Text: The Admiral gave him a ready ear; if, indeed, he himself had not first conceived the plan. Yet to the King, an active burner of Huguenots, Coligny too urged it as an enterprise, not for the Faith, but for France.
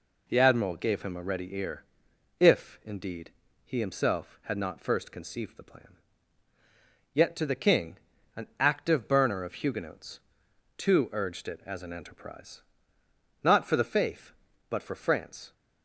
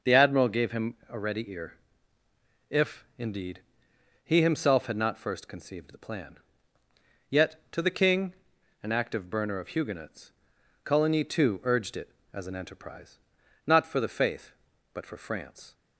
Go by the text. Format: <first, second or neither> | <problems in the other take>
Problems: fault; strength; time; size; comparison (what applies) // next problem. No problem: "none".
second | skips "Coligny"; at 10.4 s